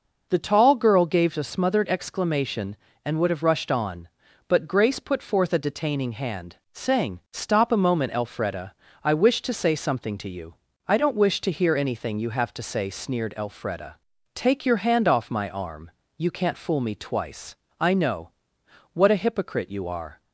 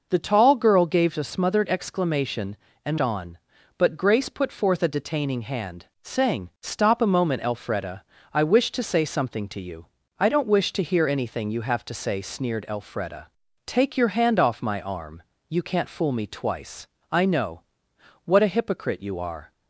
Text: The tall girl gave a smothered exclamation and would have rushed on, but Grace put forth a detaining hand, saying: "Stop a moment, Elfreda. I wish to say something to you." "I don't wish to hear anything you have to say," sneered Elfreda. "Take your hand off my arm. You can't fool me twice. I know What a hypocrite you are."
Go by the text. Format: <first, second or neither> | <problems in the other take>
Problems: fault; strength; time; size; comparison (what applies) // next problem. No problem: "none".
first | skips "would have rushed"; at 2.9 s // pauses between "know" and "What"; noticeable; at 17.6 s; 0.64 s long; noticeable in the first